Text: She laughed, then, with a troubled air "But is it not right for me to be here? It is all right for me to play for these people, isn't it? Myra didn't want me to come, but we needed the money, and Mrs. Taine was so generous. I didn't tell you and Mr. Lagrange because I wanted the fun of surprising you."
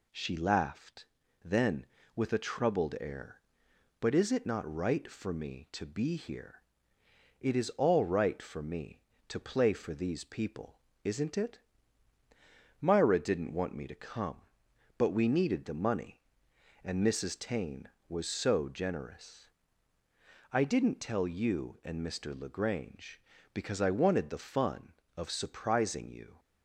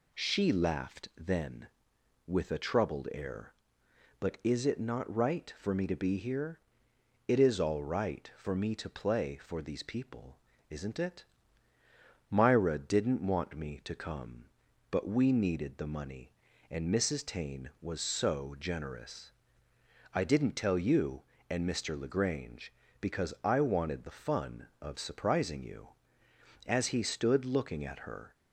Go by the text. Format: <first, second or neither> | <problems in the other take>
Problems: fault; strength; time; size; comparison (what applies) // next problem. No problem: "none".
first | goes on to say "As he stood looking at her"; strong; from 26.6 s on; 1.6 s long